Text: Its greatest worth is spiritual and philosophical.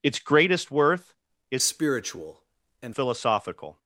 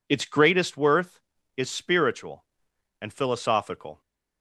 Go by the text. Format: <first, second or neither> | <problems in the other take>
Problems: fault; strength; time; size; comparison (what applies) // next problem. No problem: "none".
second | changes voice from "spiritual" to "and"; from 1.6 to 2.9 s; 1.3 s long